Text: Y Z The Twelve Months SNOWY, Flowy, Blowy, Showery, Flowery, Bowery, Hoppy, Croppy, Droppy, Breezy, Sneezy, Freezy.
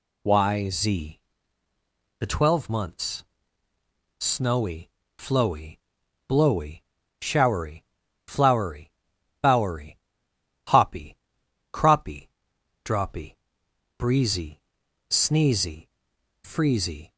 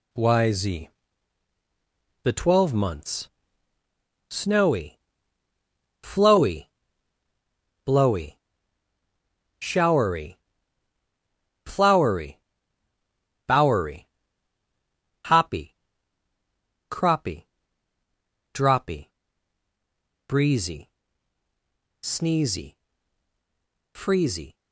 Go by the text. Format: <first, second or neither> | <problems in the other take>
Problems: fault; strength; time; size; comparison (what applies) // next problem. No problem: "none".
first | gets quieter; throughout; 7 dB // pauses between "Z" and "The"; strong; at 0.8 s; 1.3 s long; also in the first // pauses between "Months" and "SNOWY"; at 3.2 s; 1.0 s long; noticeable in the first